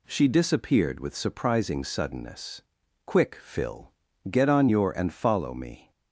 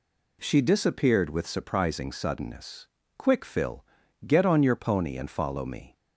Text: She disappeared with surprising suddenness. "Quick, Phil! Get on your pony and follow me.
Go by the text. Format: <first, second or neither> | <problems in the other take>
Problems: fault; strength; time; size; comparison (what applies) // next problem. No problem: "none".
second | skips "pony"; at 4.9 s